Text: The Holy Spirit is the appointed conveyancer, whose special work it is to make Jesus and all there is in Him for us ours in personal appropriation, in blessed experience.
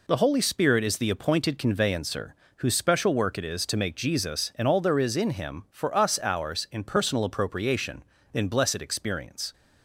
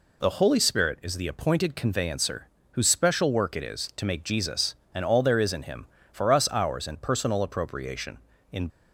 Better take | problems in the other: first | stops before "blessed experience"; at 8.6 s

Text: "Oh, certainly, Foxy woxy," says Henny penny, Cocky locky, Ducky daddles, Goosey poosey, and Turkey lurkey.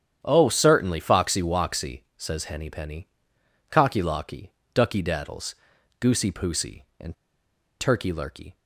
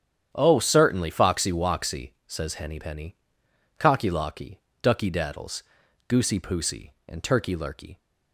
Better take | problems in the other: second | starts louder than the rest; strong; until 1.2 s; 9 dB; strong in the second // pauses between "and" and "Turkey"; noticeable; at 7.1 s; 0.64 s long

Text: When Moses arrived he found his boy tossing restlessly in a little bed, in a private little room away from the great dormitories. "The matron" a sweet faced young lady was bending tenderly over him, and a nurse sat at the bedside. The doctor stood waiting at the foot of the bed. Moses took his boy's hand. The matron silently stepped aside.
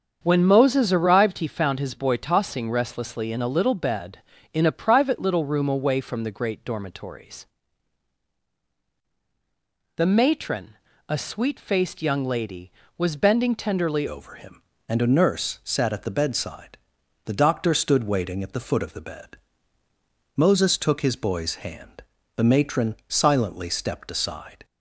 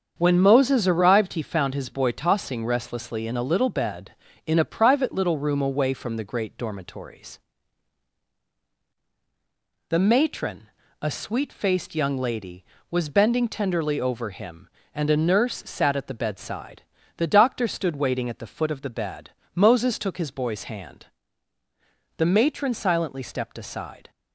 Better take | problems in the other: second | starts louder than the rest; strong; until 1.2 s; 7.5 dB; strong in the second // pauses between "matron" and "a"; slight; at 10.7 s; 0.34 s long; slight in the second // changes voice at "over"; from 14.0 s on; 10.6 s long

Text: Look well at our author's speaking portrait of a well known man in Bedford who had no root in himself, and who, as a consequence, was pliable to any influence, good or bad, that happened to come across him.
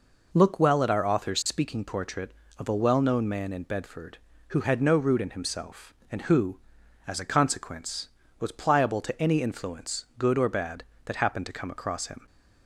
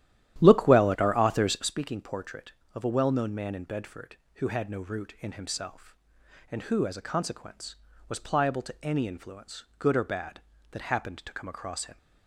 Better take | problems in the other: first | starts louder than the rest; strong; until 1.7 s; 12 dB

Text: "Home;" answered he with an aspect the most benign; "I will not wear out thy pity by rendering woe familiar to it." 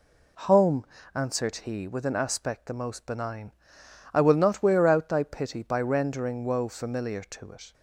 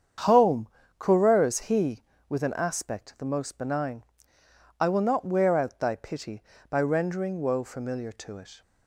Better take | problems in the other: first | starts louder than the rest; strong; until 1.5 s; 8 dB // says "coureurs" for "answered"; at 0.9 s

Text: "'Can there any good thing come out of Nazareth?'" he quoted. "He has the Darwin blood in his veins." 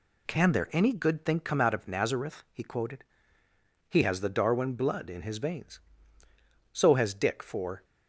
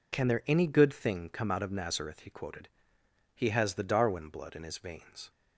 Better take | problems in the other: second | goes on to say "So has Dick for"; noticeable; from 6.7 s on; 1.1 s long

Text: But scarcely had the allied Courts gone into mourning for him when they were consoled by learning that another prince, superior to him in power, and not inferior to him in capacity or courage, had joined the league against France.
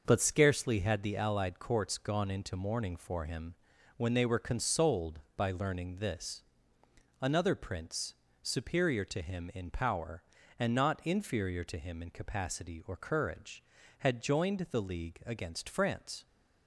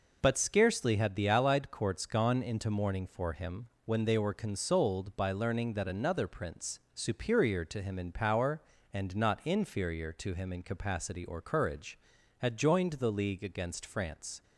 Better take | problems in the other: second | starts louder than the rest; until 1.0 s; 6 dB // pauses between "him" and "when"; at 3.5 s; 0.42 s long; slight in the second // says "this" for "that"; at 5.9 s

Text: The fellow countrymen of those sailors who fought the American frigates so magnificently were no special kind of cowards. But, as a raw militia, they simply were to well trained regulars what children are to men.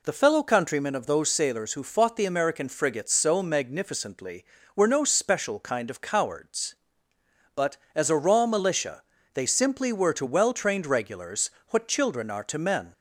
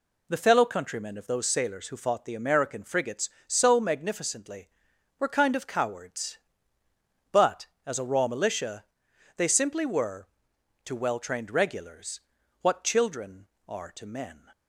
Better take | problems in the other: first | skips "no special"; at 5.2 s // pauses between "regulars" and "what"; at 12.2 s; 0.40 s long; slight in the first

